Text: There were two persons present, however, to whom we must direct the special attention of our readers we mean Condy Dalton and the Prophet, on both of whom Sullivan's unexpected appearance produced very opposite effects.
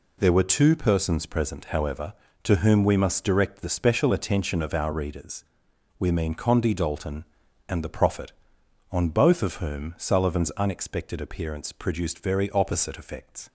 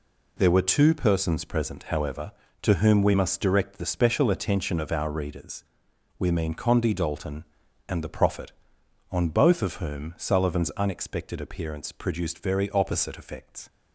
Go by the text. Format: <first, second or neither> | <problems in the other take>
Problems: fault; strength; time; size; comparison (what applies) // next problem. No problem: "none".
neither | pauses between "readers" and "we"; noticeable; the same in both